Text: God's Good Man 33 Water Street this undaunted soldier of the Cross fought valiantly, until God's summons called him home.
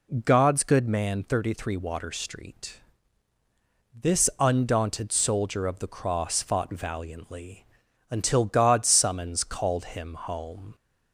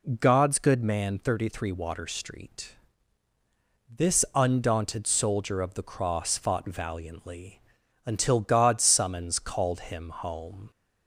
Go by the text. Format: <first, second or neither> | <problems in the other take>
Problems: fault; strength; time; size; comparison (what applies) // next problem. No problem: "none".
neither | pauses between "Street" and "this"; the same in both